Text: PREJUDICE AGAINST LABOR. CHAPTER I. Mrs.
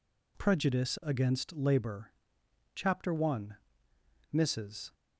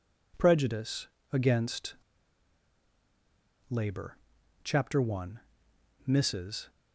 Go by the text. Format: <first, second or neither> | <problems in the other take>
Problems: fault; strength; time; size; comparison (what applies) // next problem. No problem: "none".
first | pauses between "PREJUDICE" and "AGAINST"; slight; at 1.0 s; 0.24 s long // pauses between "AGAINST" and "LABOR"; strong; at 1.9 s; 1.7 s long